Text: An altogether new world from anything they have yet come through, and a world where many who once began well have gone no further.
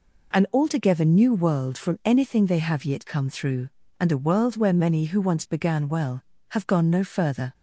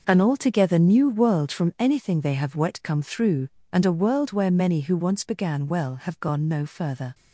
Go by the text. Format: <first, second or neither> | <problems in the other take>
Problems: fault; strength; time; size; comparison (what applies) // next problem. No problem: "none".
first | says "wet" for "yet"; at 2.5 s